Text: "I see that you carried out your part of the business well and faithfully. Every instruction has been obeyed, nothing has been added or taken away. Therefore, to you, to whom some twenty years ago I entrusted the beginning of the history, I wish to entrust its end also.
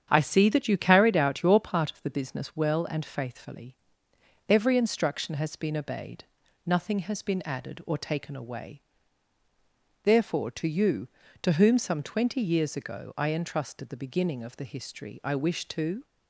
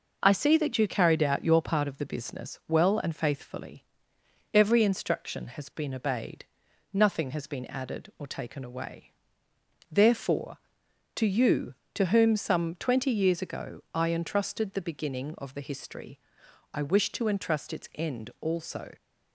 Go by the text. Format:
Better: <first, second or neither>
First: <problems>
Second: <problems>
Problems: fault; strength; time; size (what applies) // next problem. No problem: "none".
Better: second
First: starts louder than the rest; strong; until 1.1 s; 8.5 dB // stops before "entrust its end also"; at 16.0 s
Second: none